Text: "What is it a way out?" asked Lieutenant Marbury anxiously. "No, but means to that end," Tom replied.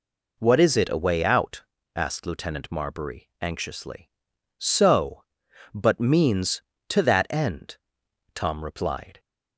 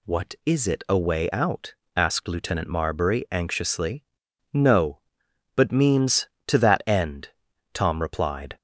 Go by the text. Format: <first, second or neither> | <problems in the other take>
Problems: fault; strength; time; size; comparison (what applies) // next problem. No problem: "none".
second | says "So" for "No"; at 4.5 s